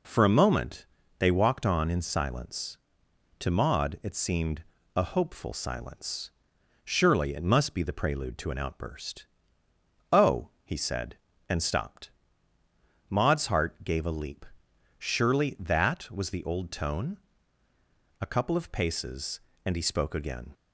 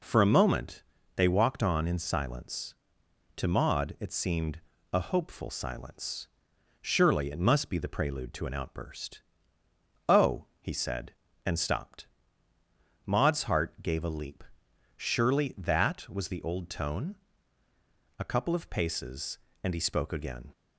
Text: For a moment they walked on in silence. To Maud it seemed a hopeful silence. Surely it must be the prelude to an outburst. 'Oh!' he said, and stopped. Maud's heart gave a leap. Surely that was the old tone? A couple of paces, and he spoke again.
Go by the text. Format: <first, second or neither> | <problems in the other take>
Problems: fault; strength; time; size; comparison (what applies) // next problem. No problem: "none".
neither | pauses between "moment" and "they"; slight; the same in both // pauses between "seemed" and "a"; slight; the same in both